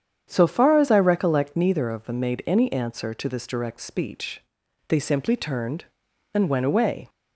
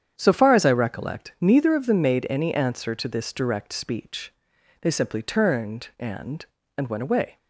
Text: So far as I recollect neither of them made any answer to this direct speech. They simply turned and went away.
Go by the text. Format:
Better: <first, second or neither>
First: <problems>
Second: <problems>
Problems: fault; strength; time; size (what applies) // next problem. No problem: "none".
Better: first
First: starts louder than the rest; strong; until 1.3 s; 8.5 dB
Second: starts louder than the rest; strong; until 1.1 s; 8.5 dB // says "and" twice; at 6.7 s